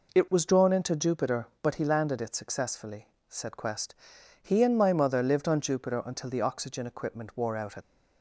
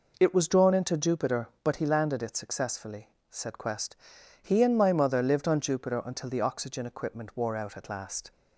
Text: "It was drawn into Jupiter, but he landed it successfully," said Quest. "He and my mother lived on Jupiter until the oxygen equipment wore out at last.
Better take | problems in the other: second | stops before "at last"; at 7.8 s

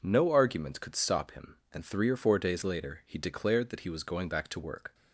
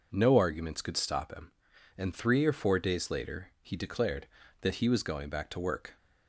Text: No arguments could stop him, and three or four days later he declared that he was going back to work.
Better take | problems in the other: neither | none

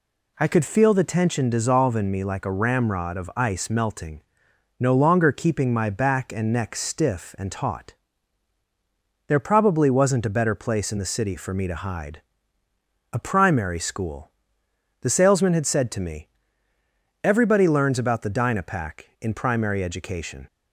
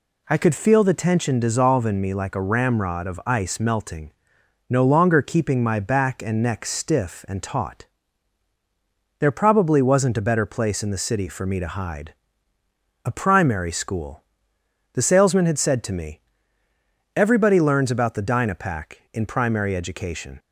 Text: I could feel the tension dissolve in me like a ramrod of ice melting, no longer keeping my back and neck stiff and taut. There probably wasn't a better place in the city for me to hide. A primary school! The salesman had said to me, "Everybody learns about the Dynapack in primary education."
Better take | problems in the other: neither | none

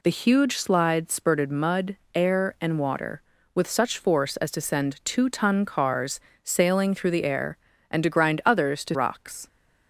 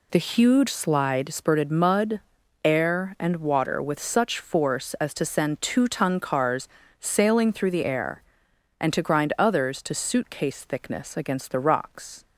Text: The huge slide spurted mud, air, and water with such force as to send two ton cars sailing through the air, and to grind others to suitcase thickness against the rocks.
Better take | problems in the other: second | pauses between "cars" and "sailing"; slight; at 6.1 s; 0.24 s long; slight in the second // skips "suitcase thickness against the"; at 8.9 s

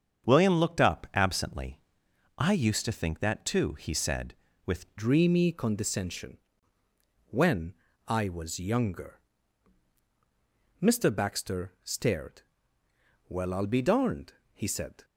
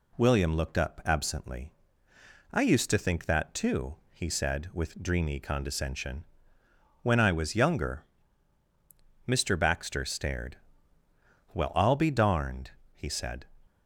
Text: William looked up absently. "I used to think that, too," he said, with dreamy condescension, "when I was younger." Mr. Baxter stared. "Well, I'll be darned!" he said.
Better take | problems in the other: second | starts louder than the rest; strong; until 1.3 s; 7 dB // changes voice at "dreamy"; from 4.9 s on; 10.1 s long // pauses between "when" and "I"; slight; at 7.7 s; 0.34 s long

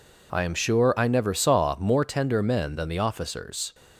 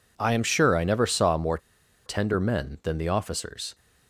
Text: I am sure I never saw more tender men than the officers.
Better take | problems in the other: first | pauses between "more" and "tender"; noticeable; at 1.5 s; 0.48 s long

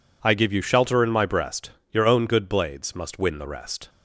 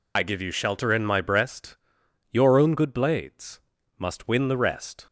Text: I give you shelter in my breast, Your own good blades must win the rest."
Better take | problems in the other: first | loses the start of "I"; at 0.1 s; 60 ms // pauses between "blades" and "must"; slight; at 3.6 s; 0.36 s long

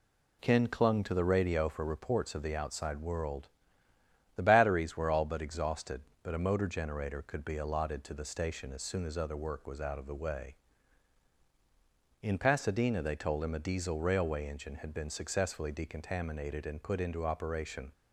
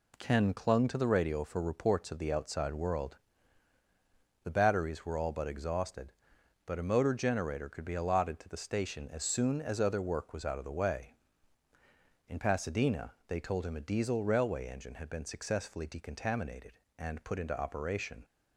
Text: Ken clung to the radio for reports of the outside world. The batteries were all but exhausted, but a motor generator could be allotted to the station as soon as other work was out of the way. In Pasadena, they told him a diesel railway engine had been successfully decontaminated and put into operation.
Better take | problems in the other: neither | none

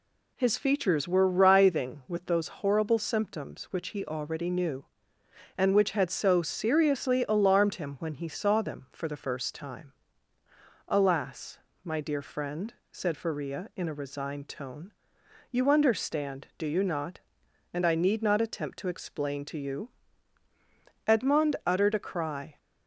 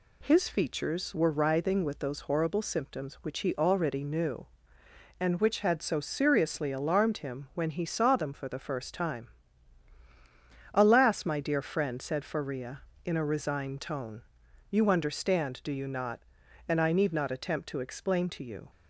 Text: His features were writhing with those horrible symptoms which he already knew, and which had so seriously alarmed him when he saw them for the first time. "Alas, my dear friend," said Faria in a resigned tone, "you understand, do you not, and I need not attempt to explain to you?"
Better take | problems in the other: second | goes on to say "Edmond uttered a cry"; from 21.0 s on; 1.5 s long

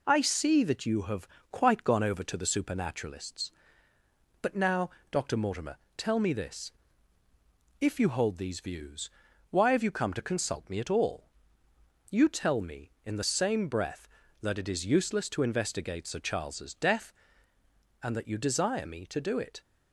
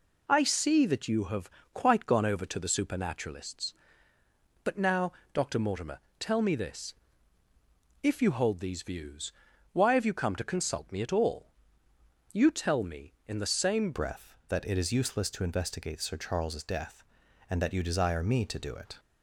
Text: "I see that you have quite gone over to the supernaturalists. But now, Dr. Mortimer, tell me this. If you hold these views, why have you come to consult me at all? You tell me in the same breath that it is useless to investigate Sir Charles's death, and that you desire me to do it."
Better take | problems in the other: first | pauses between "have" and "quite"; slight; at 1.4 s; 0.24 s long; slight in the first // changes voice at "breath"; from 13.9 s on; 5.0 s long

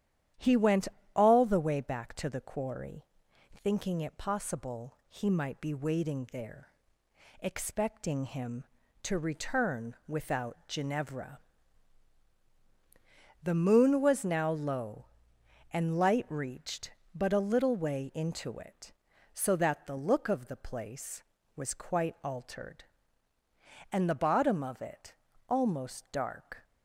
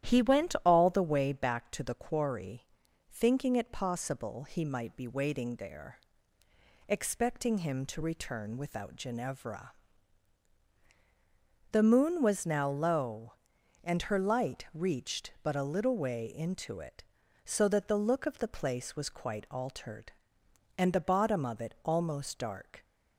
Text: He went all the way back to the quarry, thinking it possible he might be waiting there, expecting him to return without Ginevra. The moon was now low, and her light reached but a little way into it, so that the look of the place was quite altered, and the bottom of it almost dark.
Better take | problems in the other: second | starts louder than the rest; strong; until 1.6 s; 10.5 dB; strong in the second // pauses between "went" and "all"; slight; at 0.8 s; 0.26 s long // skips "her"; at 15.9 s // pauses between "it" and "almost"; slight; at 25.1 s; 0.36 s long

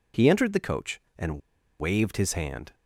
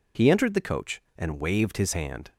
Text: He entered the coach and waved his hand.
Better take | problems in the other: second | pauses between "and" and "waved"; at 1.4 s; 0.39 s long

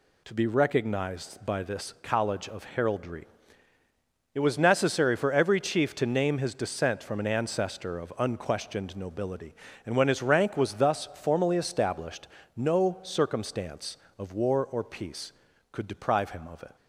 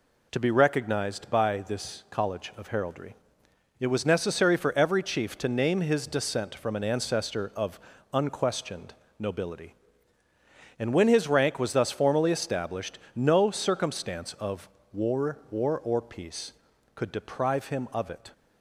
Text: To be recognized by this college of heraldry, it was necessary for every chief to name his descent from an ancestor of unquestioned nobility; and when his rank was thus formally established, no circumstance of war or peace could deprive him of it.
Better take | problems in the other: first | pauses between "of" and "unquestioned"; slight; at 7.7 s; 0.34 s long // pauses between "unquestioned" and "nobility"; slight; at 8.9 s; 0.24 s long // pauses between "of" and "war"; slight; at 14.6 s; 0.24 s long // says "war" twice; at 15.4 s

